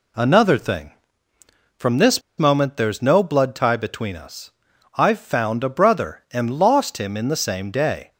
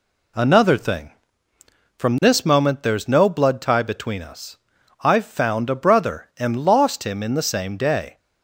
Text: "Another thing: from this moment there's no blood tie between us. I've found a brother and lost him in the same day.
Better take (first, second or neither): second